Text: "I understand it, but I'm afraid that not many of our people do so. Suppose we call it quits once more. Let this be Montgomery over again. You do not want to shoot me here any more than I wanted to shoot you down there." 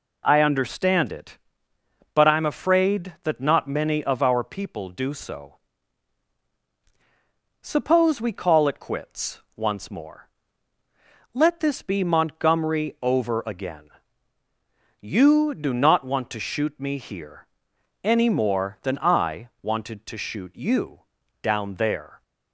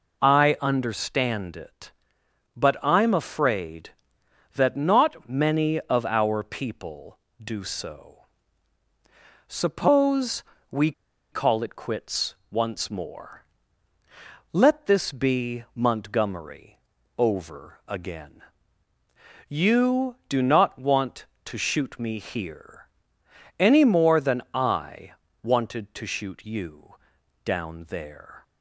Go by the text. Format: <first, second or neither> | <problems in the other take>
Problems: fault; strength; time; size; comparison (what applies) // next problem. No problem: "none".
first | pauses between "Suppose" and "we"; slight; at 10.4 s; 0.28 s long // pauses between "we" and "call"; at 10.9 s; 0.40 s long // pauses between "quits" and "once"; slight; at 12.3 s; 0.16 s long; slight in the first // pauses between "Montgomery" and "over"; at 16.7 s; 0.40 s long // pauses between "here" and "any"; noticeable; at 22.8 s; 0.72 s long; noticeable in the first // pauses between "I" and "wanted"; slight; at 25.1 s; 0.32 s long // pauses between "you" and "down"; noticeable; at 26.9 s; 0.50 s long; also in the first